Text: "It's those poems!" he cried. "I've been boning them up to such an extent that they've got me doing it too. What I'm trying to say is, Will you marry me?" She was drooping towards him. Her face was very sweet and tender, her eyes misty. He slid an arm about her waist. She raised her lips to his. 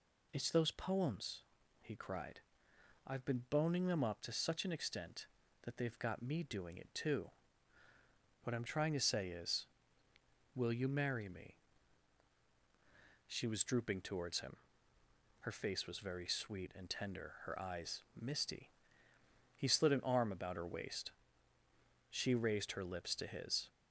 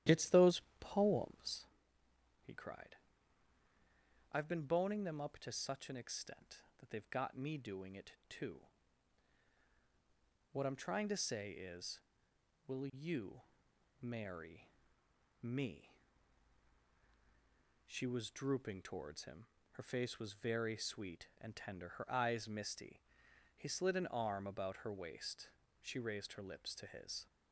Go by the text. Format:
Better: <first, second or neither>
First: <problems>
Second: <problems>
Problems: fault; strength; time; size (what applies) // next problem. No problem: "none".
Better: first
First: none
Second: starts louder than the rest; strong; until 1.7 s; 12 dB // pauses between "those" and "poems"; slight; at 0.6 s; 0.18 s long // pauses between "you" and "marry"; noticeable; at 13.4 s; 0.58 s long // pauses between "marry" and "me"; noticeable; at 14.7 s; 0.70 s long